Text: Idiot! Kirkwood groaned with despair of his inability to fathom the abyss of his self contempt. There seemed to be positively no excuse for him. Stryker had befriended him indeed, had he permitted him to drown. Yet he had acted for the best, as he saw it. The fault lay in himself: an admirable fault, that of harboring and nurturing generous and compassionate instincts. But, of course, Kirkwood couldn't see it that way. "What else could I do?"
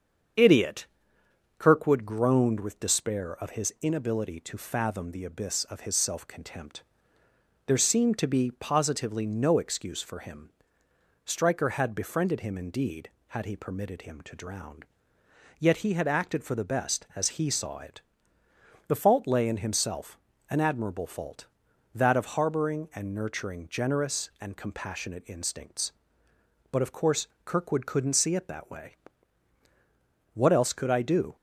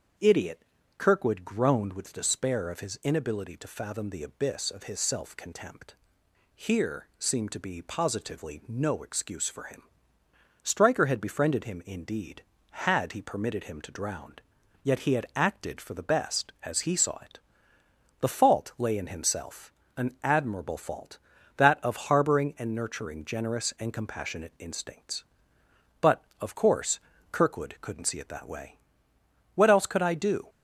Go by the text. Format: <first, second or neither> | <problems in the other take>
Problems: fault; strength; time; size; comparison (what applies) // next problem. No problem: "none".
first | starts louder than the rest; until 1.5 s; 7 dB; strong in the first // says "Here" for "There"; at 6.5 s